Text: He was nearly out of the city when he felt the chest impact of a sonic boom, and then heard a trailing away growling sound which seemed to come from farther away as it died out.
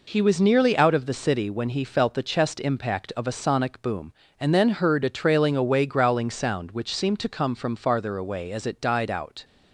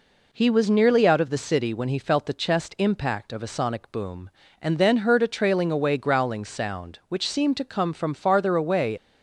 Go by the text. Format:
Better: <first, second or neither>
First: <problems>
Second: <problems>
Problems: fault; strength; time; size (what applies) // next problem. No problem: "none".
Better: first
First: none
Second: stops before "as it died out"; at 8.9 s